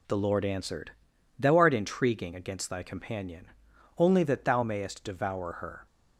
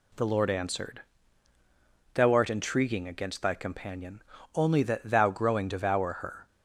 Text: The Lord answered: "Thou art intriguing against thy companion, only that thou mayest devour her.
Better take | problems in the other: first | says "growing" for "mayest"; at 5.2 s

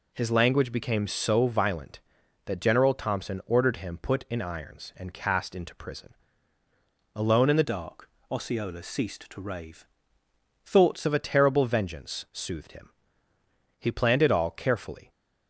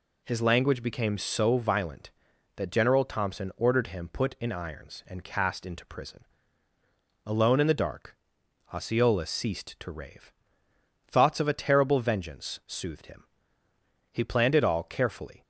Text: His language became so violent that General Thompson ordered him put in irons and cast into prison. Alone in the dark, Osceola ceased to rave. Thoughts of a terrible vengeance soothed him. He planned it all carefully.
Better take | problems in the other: second | changes voice from "dark" to "Thoughts"; from 7.6 to 11.0 s; 3.4 s long

